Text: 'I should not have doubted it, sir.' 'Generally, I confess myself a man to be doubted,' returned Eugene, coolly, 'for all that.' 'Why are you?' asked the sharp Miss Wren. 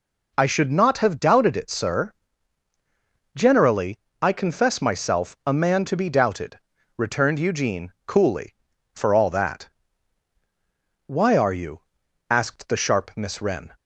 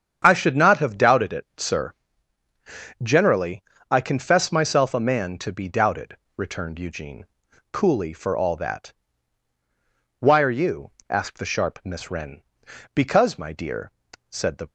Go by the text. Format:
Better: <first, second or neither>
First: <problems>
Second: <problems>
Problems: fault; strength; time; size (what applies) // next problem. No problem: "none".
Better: first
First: none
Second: starts louder than the rest; strong; until 1.2 s; 7.5 dB // goes on to say "Because my dear said the"; strong; from 12.9 s on; 1.7 s long